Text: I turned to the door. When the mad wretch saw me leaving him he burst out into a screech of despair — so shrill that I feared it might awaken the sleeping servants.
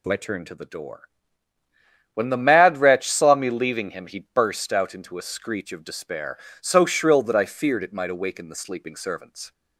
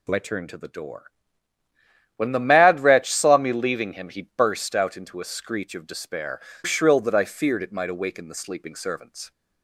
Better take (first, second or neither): first